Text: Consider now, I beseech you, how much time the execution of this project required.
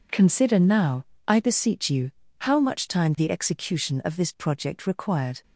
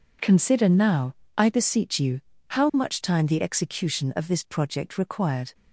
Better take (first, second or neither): neither